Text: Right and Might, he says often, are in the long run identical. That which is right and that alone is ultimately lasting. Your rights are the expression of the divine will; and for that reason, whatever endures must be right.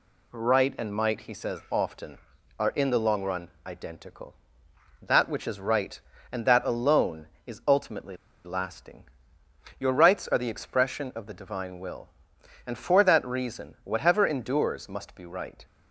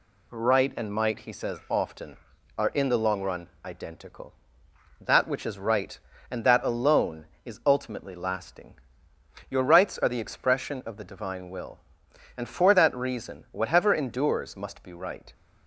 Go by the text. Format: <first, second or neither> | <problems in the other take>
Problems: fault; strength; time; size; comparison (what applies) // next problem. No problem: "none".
second | pauses between "run" and "identical"; slight; at 3.4 s; 0.18 s long; slight in the second // pauses between "ultimately" and "lasting"; slight; at 8.1 s; 0.29 s long